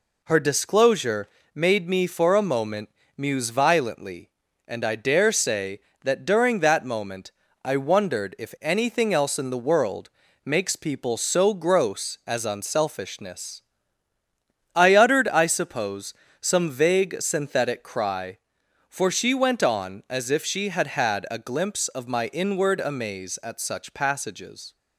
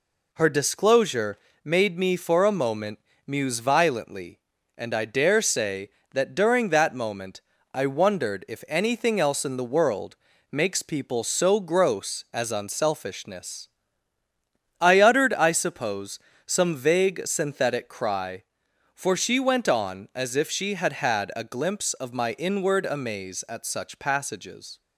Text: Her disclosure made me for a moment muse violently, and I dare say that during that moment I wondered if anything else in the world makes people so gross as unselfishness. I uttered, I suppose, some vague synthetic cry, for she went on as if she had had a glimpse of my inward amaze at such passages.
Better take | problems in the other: neither | pauses between "disclosure" and "made"; slight; the same in both // pauses between "moment" and "muse"; slight; the same in both // pauses between "moment" and "I"; slight; the same in both // pauses between "world" and "makes"; slight; the same in both

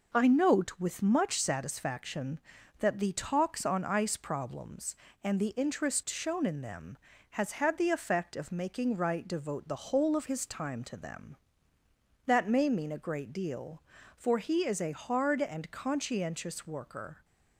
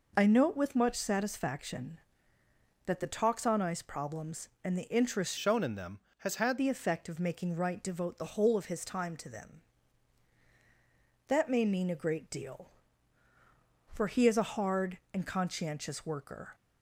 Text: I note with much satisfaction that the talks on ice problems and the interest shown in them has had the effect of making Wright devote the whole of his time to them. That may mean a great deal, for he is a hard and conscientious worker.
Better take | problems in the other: first | changes voice from "shown" to "had"; from 5.3 to 6.5 s; 1.2 s long

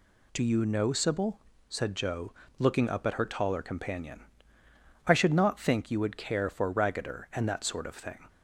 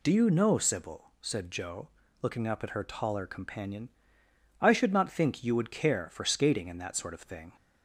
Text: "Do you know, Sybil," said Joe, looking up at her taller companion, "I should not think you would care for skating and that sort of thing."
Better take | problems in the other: second | says "raggeder" for "skating"; at 6.7 s

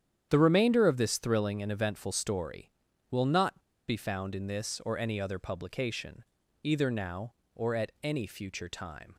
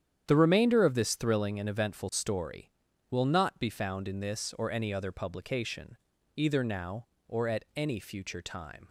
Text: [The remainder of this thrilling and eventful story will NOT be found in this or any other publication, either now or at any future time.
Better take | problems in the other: second | starts louder than the rest; strong; until 1.3 s; 9 dB; strong in the second // pauses between "NOT" and "be"; slight; at 3.5 s; 0.28 s long

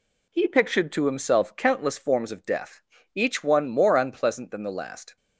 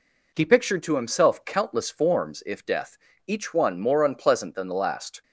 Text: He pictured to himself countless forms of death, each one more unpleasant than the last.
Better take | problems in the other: first | says "if" for "of"; at 2.4 s

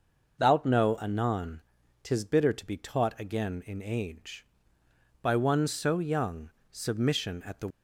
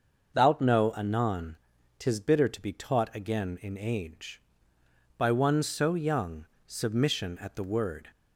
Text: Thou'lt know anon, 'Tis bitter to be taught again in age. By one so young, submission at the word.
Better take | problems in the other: second | starts louder than the rest; noticeable; until 1.4 s; 6 dB; also in the second // stops before "word"; at 7.6 s

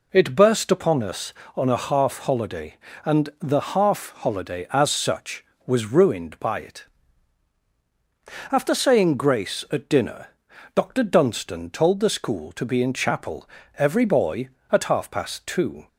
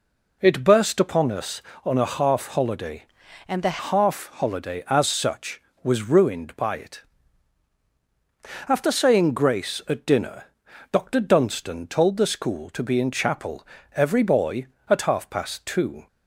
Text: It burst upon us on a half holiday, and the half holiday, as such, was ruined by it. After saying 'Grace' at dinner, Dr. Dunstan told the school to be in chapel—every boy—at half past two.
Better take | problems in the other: first | changes voice from "and" to "the"; from 3.4 to 3.7 s; 0.3 s long

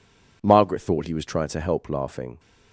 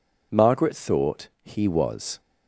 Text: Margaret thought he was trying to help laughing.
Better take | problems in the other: first | pauses between "thought" and "he"; slight; at 1.2 s; 0.16 s long // stops before "trying to help laughing"; at 2.1 s

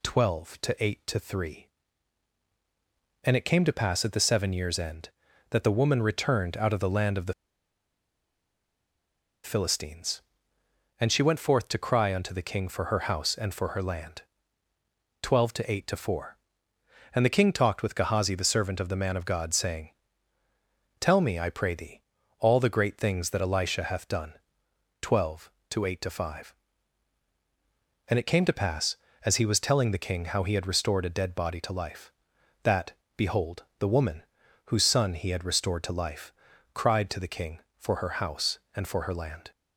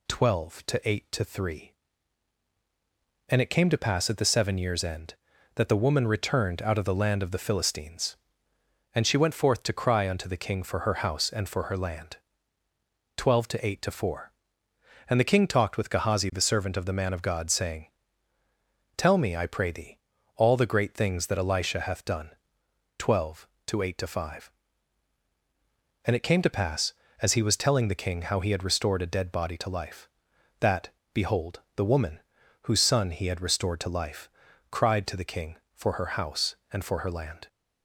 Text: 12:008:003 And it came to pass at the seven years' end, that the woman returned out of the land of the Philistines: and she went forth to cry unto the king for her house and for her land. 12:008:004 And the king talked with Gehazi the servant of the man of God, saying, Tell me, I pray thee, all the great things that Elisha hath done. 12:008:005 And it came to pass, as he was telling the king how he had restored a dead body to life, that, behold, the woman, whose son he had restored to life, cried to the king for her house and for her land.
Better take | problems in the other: second | pauses between "the" and "Philistines"; strong; at 7.3 s; 2.1 s long

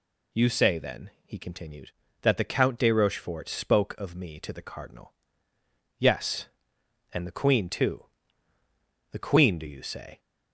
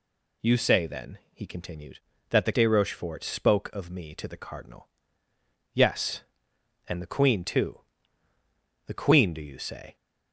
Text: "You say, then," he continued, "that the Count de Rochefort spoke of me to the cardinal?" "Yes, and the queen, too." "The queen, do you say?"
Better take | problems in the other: first | skips "Count"; at 2.5 s

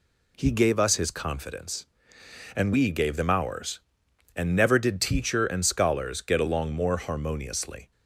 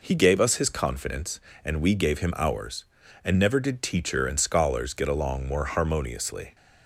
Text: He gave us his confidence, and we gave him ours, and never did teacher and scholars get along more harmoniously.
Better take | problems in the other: second | says "them" for "him"; at 3.1 s

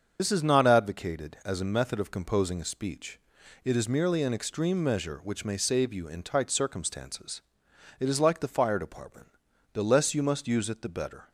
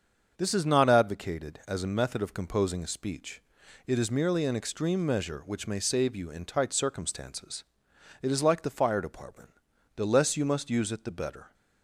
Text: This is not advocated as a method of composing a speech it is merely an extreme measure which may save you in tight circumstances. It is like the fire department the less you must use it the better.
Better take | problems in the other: second | loses the start of "This"; at 0.1 s; 50 ms // starts louder than the rest; until 1.2 s; 7 dB; also in the second // pauses between "speech" and "it"; noticeable; at 3.1 s; 0.46 s long; noticeable in the second // pauses between "department" and "the"; noticeable; at 9.2 s; 0.46 s long; noticeable in the second

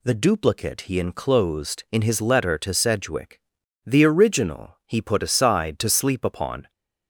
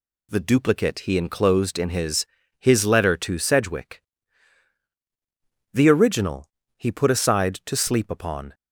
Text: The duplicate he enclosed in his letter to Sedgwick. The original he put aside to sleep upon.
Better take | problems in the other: first | says "his" twice; at 2.5 s // pauses between "original" and "he"; slight; at 6.4 s; 0.30 s long

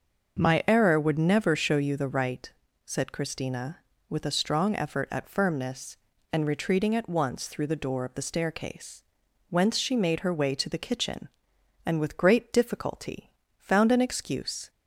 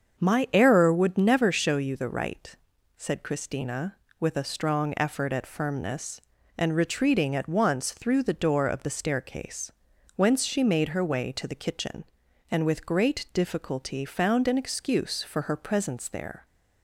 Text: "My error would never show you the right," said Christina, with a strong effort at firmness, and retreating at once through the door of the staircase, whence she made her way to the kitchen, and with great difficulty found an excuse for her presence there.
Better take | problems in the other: second | starts louder than the rest; until 1.4 s; 6.5 dB; also in the second // pauses between "difficulty" and "found"; slight; at 13.3 s; 0.26 s long // stops before "for her presence there"; at 14.6 s

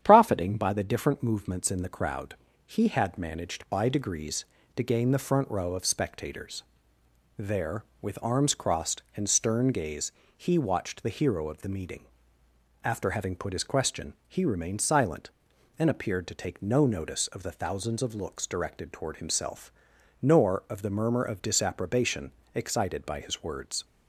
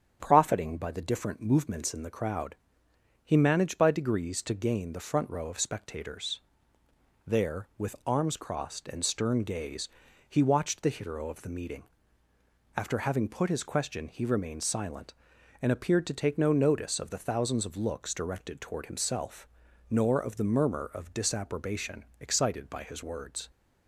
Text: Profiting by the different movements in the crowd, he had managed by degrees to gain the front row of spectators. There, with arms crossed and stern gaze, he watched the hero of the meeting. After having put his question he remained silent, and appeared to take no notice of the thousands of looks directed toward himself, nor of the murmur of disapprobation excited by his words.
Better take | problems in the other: first | starts louder than the rest; strong; until 1.2 s; 8.5 dB; strong in the first // skips "had"; at 3.3 s // pauses between "disapprobation" and "excited"; slight; at 22.0 s; 0.16 s long; slight in the first

